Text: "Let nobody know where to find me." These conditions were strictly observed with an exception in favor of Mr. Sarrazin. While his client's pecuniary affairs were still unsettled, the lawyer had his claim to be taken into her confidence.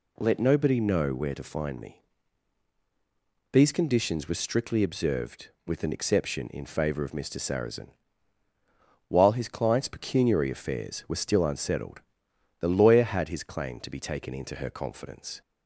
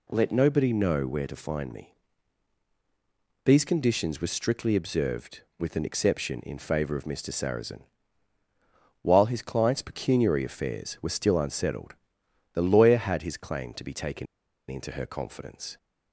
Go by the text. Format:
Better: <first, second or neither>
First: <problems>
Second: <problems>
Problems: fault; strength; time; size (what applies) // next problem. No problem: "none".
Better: first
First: none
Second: pauses between "taken" and "into"; at 14.2 s; 0.43 s long